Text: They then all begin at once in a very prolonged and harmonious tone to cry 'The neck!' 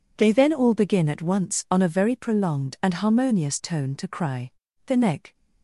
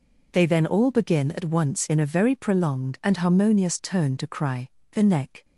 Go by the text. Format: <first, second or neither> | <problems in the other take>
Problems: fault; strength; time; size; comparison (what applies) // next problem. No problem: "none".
second | says "on" for "in"; at 1.7 s // pauses between "cry" and "The"; slight; at 4.5 s; 0.34 s long; slight in the second